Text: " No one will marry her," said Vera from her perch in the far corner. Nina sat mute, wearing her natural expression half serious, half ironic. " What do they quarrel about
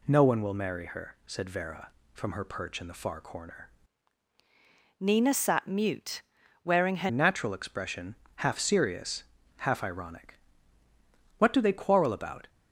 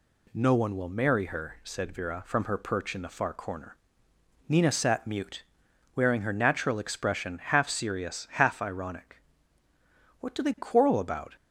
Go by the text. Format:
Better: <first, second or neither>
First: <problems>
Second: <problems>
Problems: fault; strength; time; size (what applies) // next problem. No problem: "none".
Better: second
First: changes voice from "Nina" to "her"; from 4.9 to 7.0 s; 2.1 s long // pauses between "expression" and "half"; slight; at 8.1 s; 0.20 s long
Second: none